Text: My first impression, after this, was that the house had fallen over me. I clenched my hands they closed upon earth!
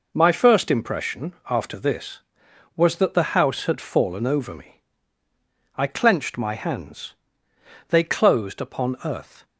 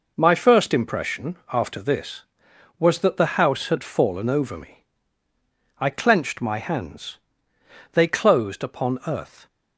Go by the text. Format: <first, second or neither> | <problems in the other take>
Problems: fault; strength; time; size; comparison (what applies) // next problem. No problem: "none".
neither | pauses between "hands" and "they"; noticeable; the same in both